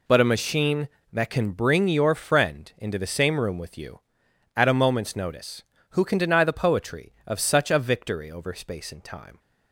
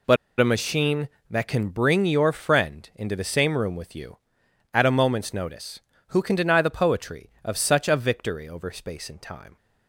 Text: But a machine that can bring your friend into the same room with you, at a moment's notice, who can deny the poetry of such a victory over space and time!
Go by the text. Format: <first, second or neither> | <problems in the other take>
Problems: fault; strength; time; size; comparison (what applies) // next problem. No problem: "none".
first | pauses between "But" and "a"; slight; at 0.1 s; 0.23 s long